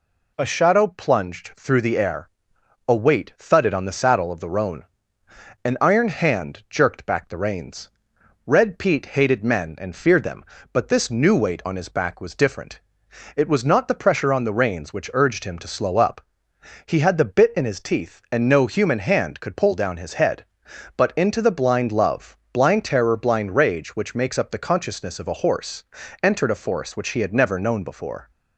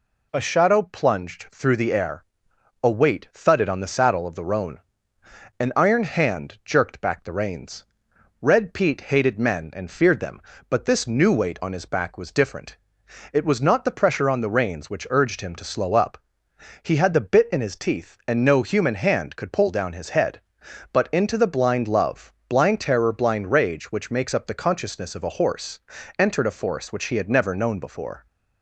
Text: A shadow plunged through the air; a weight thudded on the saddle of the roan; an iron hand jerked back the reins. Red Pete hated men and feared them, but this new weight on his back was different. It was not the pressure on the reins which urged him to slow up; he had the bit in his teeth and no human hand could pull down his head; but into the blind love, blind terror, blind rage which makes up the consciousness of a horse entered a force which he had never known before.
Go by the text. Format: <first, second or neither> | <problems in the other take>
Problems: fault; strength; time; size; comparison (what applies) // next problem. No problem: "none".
neither | pauses between "horse" and "entered"; the same in both